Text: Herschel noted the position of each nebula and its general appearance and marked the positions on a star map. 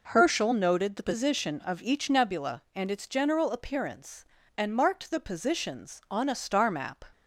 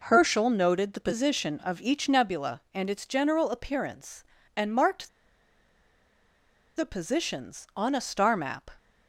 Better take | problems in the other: first | pauses between "marked" and "the"; strong; at 5.0 s; 1.6 s long

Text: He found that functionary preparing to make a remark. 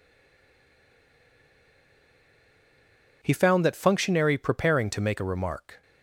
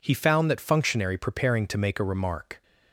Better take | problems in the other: second | stays silent before the first word; strong; until 3.2 s; 3.2 s long

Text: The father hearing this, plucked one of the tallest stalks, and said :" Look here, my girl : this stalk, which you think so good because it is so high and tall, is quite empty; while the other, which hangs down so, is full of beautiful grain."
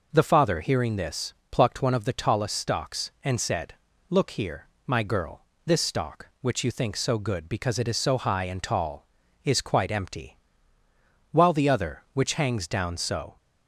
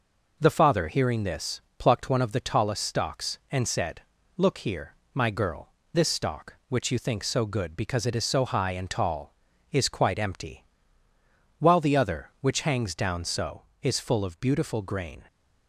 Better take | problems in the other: second | stops before "is full of beautiful grain"; at 13.3 s

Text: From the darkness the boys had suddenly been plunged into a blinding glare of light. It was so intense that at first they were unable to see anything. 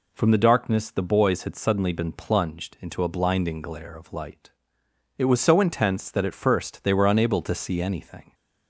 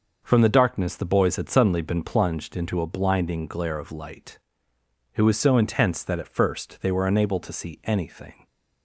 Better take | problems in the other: neither | none

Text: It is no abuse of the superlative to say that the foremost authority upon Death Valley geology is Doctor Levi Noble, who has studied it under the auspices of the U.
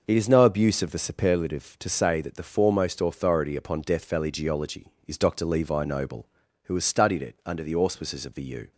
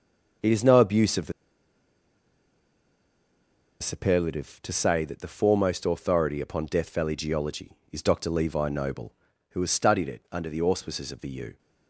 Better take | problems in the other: first | pauses between "the" and "superlative"; strong; at 1.3 s; 2.4 s long

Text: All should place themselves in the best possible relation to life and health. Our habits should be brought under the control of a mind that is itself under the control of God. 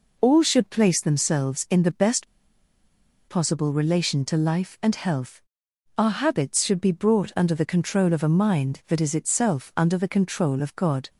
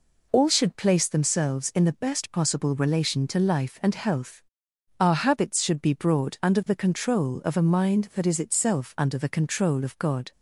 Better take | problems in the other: second | pauses between "best" and "possible"; at 2.2 s; 1.0 s long

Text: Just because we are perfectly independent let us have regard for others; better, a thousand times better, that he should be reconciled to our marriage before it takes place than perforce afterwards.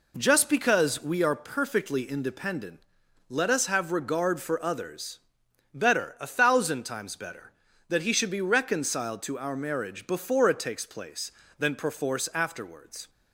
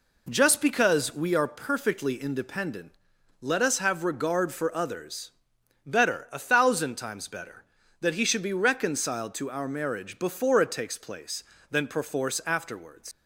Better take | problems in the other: first | pauses between "independent" and "let"; noticeable; at 2.9 s; 0.48 s long; noticeable in the first // leaves "afterwards" unfinished; at 13.1 s; 100 ms

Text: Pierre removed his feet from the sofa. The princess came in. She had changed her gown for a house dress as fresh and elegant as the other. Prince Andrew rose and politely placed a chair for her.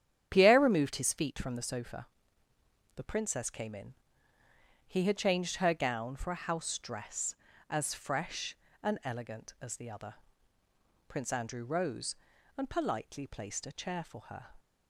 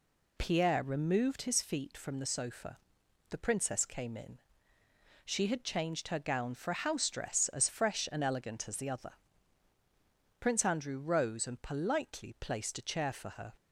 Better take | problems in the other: second | starts louder than the rest; strong; until 1.3 s; 9.5 dB // says "He" for "She"; at 4.8 s

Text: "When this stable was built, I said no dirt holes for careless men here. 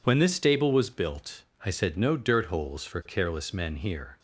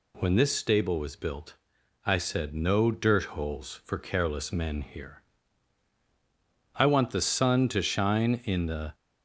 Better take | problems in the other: first | goes on to say "I want the sun to shine in the"; strong; from 6.7 s on; 2.1 s long

